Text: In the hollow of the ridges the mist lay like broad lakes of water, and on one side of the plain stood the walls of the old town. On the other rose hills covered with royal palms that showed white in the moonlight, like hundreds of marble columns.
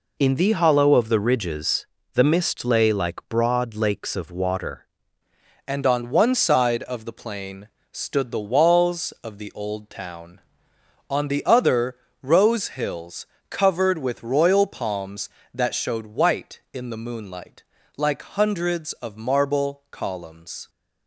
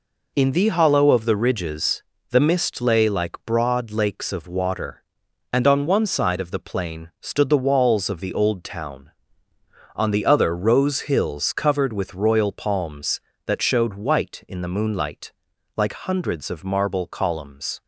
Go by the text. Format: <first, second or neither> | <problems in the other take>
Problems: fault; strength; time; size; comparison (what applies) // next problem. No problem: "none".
second | pauses between "ridges" and "the"; slight; at 1.8 s; 0.30 s long; slight in the second // changes voice at "and"; from 5.6 s on; 15.0 s long // pauses between "plain" and "stood"; slight; at 7.6 s; 0.24 s long // pauses between "other" and "rose"; slight; at 11.9 s; 0.24 s long // pauses between "hills" and "covered"; slight; at 13.2 s; 0.24 s long